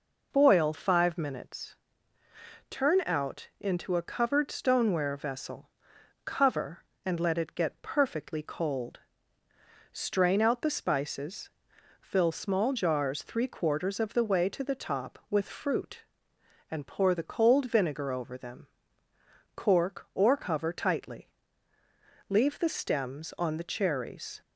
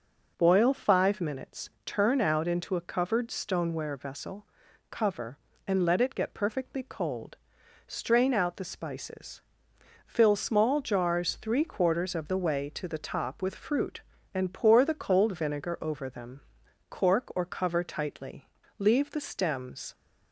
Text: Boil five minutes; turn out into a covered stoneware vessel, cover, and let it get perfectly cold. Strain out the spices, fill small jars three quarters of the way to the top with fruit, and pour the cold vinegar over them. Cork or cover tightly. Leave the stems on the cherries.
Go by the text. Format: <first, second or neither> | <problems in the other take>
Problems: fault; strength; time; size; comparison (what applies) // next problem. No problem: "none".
first | stops before "on the cherries"; at 19.9 s